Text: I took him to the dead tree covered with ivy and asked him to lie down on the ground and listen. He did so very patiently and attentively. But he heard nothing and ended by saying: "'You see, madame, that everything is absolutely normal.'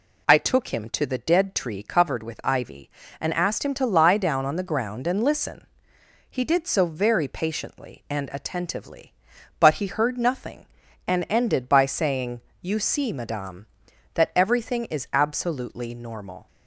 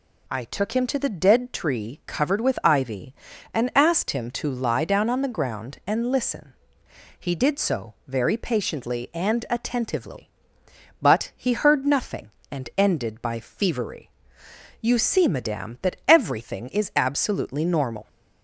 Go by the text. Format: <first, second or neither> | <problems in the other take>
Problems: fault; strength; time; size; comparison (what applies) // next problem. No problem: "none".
first | says "fevery" for "saying"; at 13.3 s